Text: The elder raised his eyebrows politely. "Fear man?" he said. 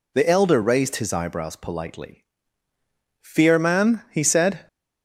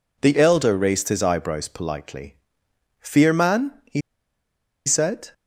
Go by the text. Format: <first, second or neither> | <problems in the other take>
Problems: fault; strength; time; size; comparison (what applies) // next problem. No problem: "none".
first | pauses between "he" and "said"; noticeable; at 4.0 s; 0.86 s long